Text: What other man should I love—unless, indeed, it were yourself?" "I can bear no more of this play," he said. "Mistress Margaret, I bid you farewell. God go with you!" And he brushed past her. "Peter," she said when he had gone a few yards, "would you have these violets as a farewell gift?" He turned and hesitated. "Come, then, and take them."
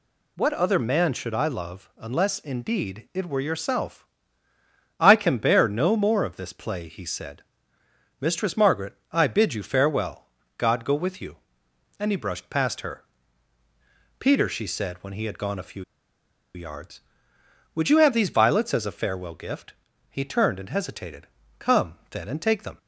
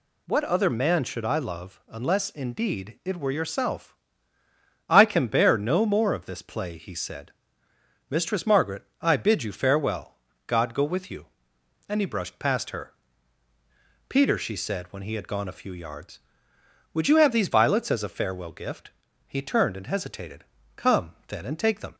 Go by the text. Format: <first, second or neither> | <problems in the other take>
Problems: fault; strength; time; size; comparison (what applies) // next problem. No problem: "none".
second | pauses between "few" and "yards"; noticeable; at 15.8 s; 0.71 s long